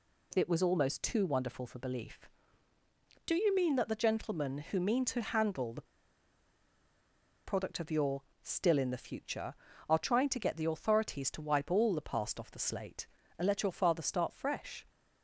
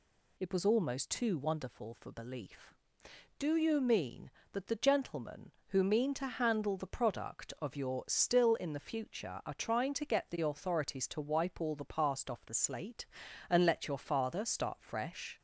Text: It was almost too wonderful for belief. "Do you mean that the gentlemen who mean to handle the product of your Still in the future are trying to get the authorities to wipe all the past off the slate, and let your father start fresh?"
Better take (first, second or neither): second